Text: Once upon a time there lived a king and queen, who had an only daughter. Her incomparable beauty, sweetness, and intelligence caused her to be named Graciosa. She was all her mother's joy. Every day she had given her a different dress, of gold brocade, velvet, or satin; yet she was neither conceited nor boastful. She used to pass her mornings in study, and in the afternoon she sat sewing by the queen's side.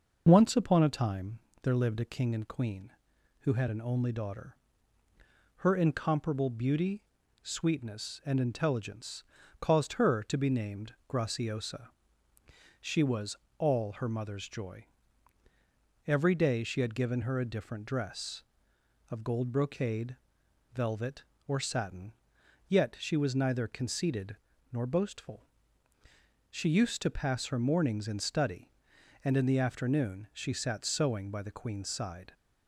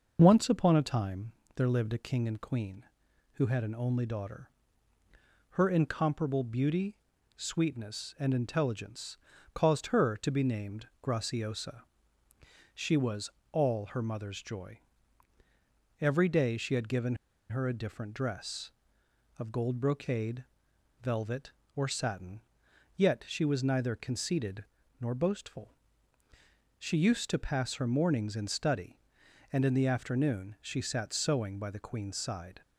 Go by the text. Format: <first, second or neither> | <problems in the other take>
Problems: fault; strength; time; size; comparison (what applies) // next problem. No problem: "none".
first | pauses between "time" and "there"; slight; at 1.3 s; 0.24 s long; slight in the first // pauses between "intelligence" and "caused"; at 9.1 s; 0.38 s long; also in the first // pauses between "was" and "all"; slight; at 13.3 s; 0.20 s long; slight in the first // pauses between "given" and "her"; slight; at 17.1 s; 0.35 s long // pauses between "conceited" and "nor"; slight; at 24.6 s; 0.36 s long; slight in the first